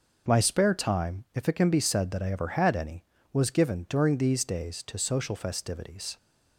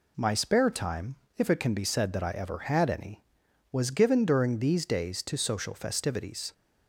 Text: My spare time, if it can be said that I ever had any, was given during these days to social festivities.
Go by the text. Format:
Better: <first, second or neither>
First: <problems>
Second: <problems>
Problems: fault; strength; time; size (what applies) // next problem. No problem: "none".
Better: neither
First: none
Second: none